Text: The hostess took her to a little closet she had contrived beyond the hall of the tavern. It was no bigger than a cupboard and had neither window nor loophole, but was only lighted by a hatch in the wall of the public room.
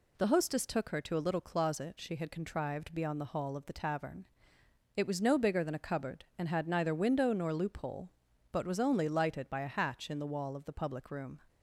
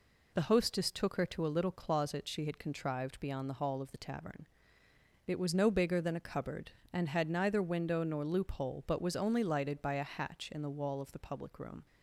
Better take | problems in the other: neither | none

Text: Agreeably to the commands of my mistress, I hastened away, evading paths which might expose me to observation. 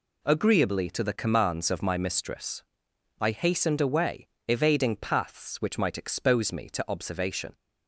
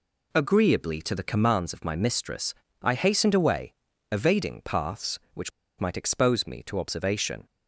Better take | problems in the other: first | pauses between "which" and "might"; slight; at 5.5 s; 0.29 s long

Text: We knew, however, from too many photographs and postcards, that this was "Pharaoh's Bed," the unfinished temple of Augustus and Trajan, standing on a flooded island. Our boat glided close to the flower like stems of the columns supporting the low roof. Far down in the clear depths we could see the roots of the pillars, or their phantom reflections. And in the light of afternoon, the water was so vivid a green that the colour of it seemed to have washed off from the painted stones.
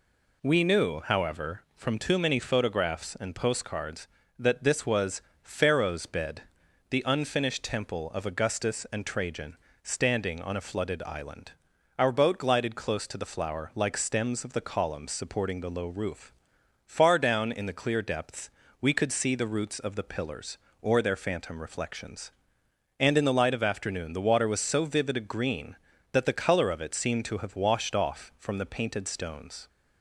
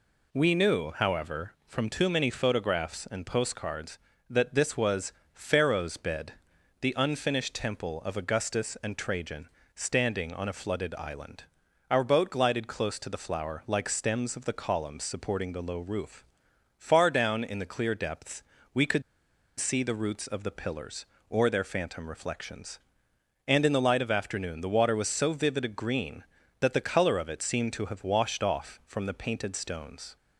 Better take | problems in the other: first | pauses between "was" and "Pharaoh's"; slight; at 5.1 s; 0.20 s long; slight in the first // pauses between "depths" and "we"; slight; at 18.4 s; 0.28 s long; slight in the first // pauses between "could" and "see"; noticeable; at 19.0 s; 0.57 s long

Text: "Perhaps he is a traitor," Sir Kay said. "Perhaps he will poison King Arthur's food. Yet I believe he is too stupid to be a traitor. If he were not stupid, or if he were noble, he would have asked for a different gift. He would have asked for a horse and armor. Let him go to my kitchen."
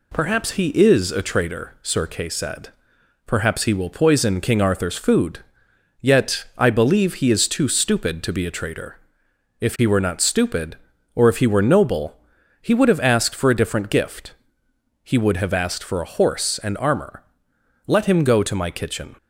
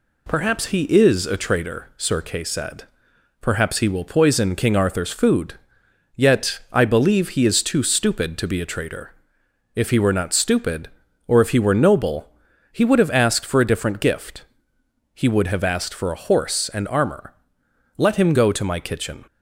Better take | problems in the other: neither | none

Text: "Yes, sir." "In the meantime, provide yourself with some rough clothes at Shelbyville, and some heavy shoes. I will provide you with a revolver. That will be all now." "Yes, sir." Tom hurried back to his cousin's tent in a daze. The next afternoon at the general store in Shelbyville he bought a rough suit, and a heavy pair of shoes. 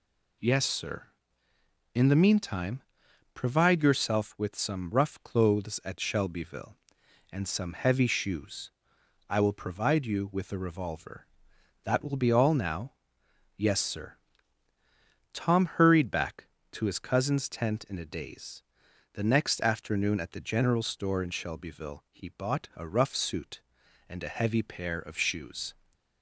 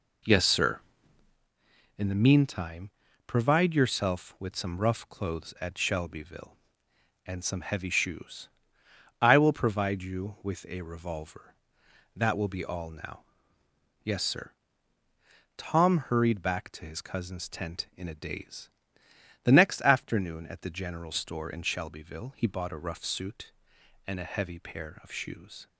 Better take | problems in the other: first | starts louder than the rest; noticeable; until 1.5 s; 4 dB

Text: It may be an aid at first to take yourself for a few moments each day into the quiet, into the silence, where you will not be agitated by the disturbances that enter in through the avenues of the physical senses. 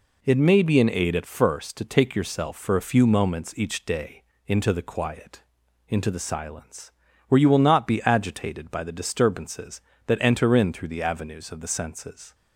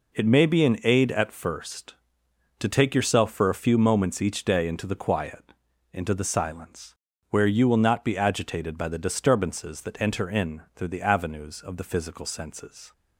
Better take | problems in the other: second | pauses between "day" and "into"; slight; at 4.2 s; 0.24 s long // skips "physical"; at 11.6 s

